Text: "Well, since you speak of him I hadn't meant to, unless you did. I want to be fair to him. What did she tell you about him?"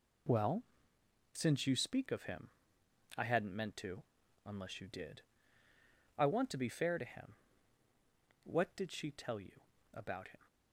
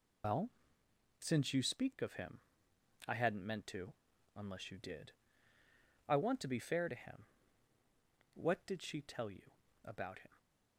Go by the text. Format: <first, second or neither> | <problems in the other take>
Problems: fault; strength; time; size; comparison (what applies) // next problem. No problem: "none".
first | loses the start of "Well"; at 0.2 s; 115 ms // pauses between "him" and "I"; noticeable; at 2.3 s; 0.68 s long; noticeable in the first // pauses between "you" and "about"; slight; at 9.5 s; 0.34 s long; slight in the first